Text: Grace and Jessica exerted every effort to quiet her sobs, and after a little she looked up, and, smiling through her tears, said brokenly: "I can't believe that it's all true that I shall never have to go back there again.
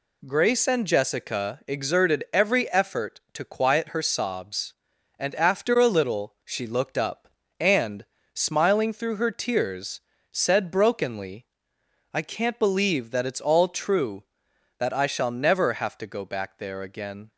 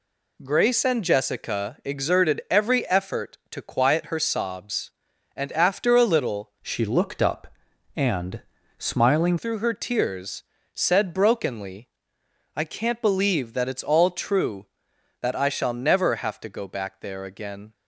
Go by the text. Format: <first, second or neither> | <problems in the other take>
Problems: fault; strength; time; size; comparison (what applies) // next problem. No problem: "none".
first | changes voice from "she" to "smiling"; from 6.6 to 9.3 s; 2.7 s long